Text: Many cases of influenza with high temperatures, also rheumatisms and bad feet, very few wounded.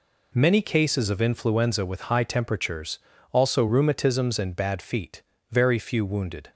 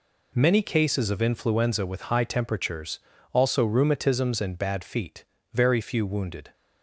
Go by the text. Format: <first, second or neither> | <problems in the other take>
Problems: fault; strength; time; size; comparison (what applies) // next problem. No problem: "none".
neither | none